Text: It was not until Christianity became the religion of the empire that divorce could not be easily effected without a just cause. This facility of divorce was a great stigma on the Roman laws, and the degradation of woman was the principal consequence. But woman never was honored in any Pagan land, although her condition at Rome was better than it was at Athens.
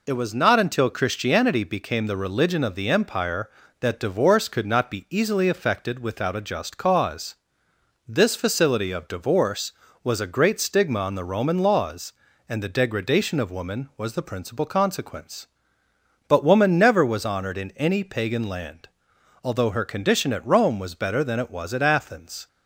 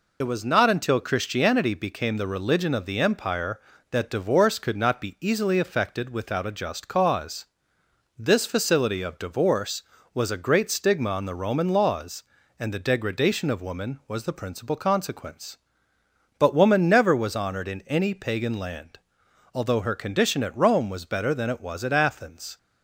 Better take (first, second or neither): first